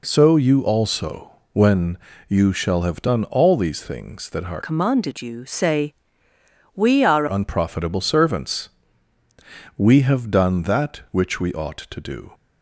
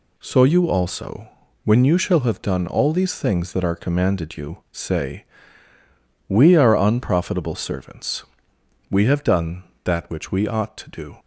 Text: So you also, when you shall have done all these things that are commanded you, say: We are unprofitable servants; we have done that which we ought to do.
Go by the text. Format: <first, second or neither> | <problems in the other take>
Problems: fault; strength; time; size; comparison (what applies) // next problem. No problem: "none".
second | pauses between "when" and "you"; slight; at 1.9 s; 0.32 s long // changes voice from "commanded" to "are"; from 4.6 to 7.2 s; 2.6 s long